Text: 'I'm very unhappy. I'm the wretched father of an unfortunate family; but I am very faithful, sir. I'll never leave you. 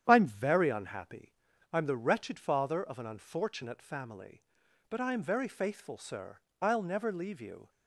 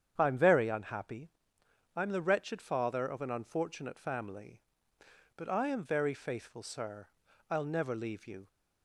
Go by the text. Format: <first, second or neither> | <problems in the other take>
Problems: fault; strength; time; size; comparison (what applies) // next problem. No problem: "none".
neither | starts louder than the rest; strong; the same in both